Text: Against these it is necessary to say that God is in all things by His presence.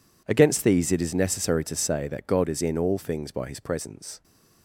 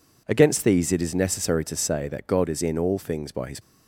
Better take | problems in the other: first | stops before "presence"; at 3.6 s

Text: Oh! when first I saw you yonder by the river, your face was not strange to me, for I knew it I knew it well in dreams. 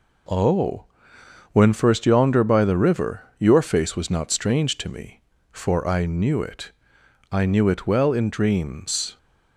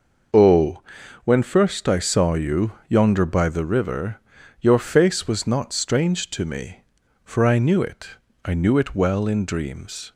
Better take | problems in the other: second | skips "I saw you"; at 2.0 s // pauses between "it" and "I"; noticeable; at 6.7 s; 0.60 s long; slight in the second

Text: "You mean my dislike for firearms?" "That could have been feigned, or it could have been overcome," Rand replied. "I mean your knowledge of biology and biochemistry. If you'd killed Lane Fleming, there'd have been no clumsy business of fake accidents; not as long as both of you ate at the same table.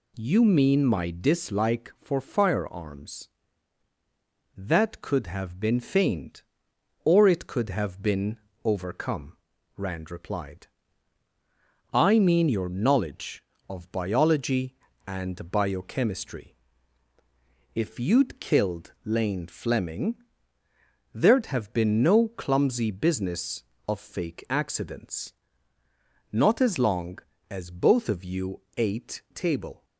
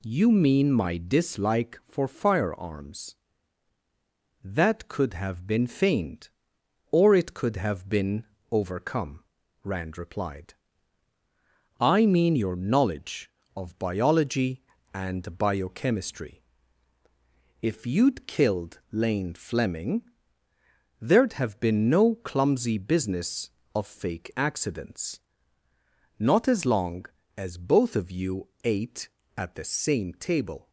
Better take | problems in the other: second | pauses between "been" and "overcome"; slight; at 8.3 s; 0.26 s long; slight in the second // pauses between "you" and "ate"; slight; at 28.6 s; 0.16 s long; slight in the second // skips "at the same"; at 29.2 s

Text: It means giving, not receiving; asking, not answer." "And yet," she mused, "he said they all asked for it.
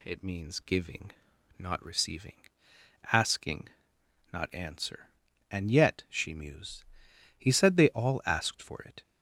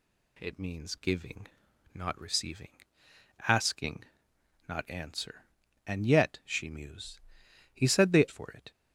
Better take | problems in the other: first | skips "all asked"; at 8.2 s

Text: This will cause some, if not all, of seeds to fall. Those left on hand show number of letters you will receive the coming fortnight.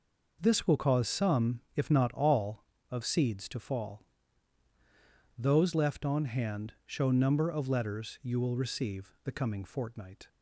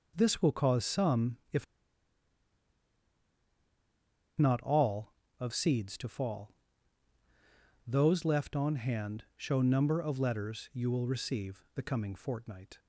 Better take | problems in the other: first | pauses between "if" and "not"; strong; at 1.6 s; 2.7 s long

